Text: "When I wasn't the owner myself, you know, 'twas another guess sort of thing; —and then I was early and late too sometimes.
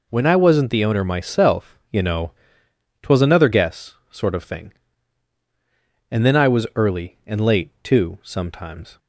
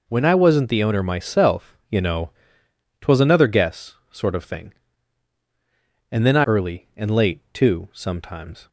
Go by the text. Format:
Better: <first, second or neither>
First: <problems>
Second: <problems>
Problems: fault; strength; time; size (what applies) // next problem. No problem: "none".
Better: first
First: none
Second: skips "was"; at 6.4 s